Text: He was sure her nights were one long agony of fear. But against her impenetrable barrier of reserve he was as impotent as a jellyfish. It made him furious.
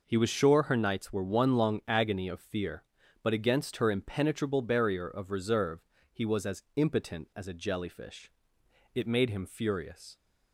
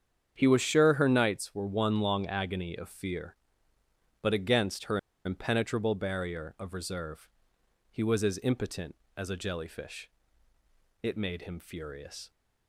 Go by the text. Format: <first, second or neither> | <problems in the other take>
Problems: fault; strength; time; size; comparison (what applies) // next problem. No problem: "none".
first | starts louder than the rest; strong; until 1.3 s; 8 dB // pauses between "her" and "impenetrable"; slight; at 4.9 s; 0.26 s long // pauses between "reserve" and "he"; noticeable; at 7.2 s; 0.62 s long; slight in the first